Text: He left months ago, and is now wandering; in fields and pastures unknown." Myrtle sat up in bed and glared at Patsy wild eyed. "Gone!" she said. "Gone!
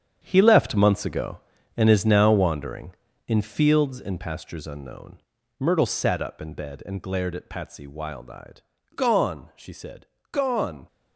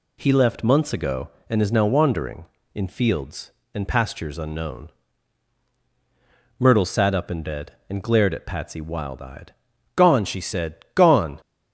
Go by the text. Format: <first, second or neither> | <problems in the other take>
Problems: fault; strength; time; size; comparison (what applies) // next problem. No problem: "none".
second | gets quieter; strong; throughout; 10.5 dB